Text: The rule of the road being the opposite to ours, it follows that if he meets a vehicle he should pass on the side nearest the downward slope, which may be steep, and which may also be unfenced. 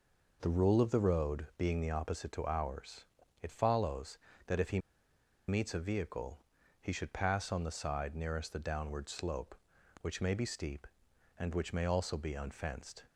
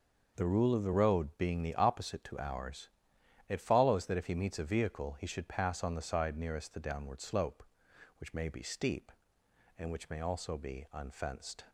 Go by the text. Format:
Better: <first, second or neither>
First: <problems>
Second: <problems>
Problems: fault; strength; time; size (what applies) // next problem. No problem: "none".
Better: second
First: pauses between "he" and "meets"; noticeable; at 4.7 s; 0.69 s long // pauses between "vehicle" and "he"; noticeable; at 6.3 s; 0.46 s long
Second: none